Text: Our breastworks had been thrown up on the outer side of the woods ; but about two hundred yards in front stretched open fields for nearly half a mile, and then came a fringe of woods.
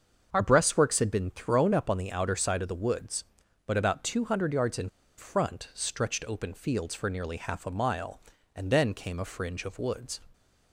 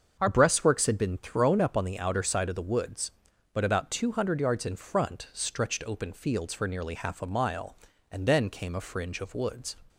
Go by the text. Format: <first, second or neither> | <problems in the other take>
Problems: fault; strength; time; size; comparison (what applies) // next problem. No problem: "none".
second | starts louder than the rest; until 1.3 s; 6.5 dB; also in the second // pauses between "in" and "front"; slight; at 4.8 s; 0.29 s long